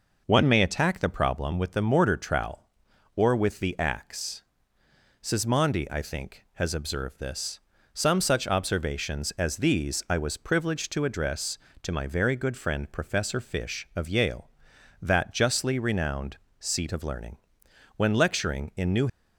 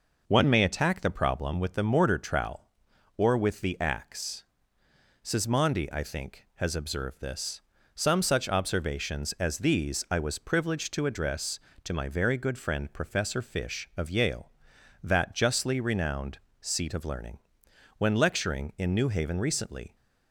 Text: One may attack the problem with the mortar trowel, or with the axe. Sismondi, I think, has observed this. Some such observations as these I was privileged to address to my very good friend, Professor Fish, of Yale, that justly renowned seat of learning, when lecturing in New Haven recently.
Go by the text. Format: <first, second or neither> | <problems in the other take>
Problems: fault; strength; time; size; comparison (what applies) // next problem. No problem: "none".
second | pauses between "renowned" and "seat"; slight; at 16.3 s; 0.20 s long; slight in the second // stops before "Haven recently"; at 19.0 s